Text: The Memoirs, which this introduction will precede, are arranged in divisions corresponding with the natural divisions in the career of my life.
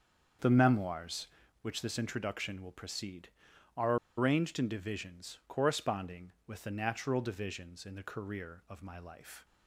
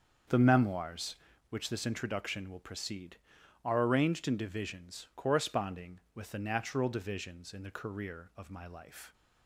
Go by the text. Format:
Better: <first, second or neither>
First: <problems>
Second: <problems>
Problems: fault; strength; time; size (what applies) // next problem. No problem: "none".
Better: second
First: starts louder than the rest; until 1.7 s; 7 dB // pauses between "are" and "arranged"; slight; at 3.9 s; 0.21 s long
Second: starts louder than the rest; until 1.6 s; 7 dB